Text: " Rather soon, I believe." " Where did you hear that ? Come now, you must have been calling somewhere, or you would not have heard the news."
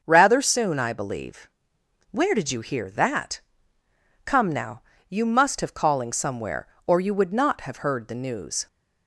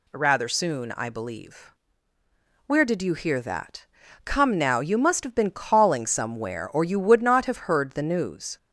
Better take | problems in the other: second | starts louder than the rest; until 1.0 s; 6.5 dB // skips "been"; at 5.7 s

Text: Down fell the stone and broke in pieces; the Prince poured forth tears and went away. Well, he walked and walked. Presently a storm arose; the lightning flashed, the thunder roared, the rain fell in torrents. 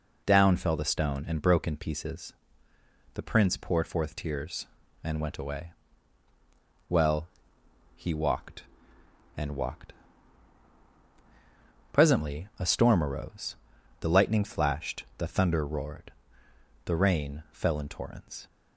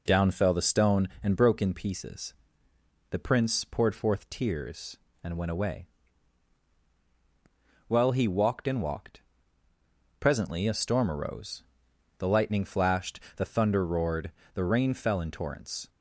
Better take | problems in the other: neither | none

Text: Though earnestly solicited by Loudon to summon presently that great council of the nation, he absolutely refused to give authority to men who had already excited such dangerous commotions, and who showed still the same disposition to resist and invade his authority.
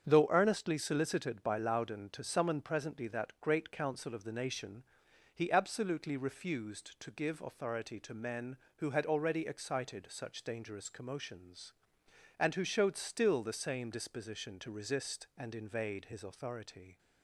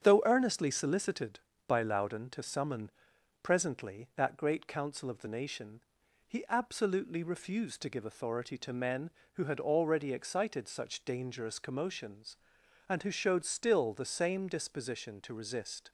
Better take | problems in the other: first | starts louder than the rest; strong; until 1.0 s; 8.5 dB; strong in the first // pauses between "summon" and "presently"; noticeable; at 2.9 s; 0.50 s long // stops before "and invade his authority"; at 15.8 s

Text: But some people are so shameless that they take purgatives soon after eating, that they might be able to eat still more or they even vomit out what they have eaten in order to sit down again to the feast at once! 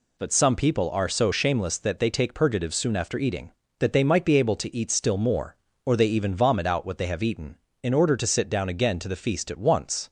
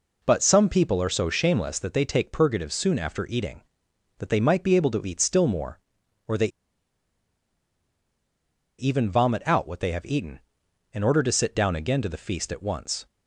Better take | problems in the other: first | pauses between "they" and "even"; strong; at 6.4 s; 2.3 s long

